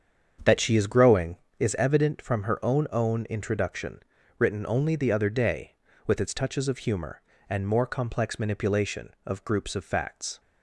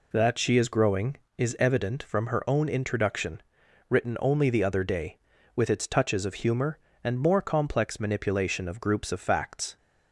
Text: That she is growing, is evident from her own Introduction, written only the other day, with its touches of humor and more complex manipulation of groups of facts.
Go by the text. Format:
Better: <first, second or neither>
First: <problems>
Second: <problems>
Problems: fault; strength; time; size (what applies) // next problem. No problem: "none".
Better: second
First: starts louder than the rest; strong; until 1.6 s; 7.5 dB // says "own" twice; at 2.9 s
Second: none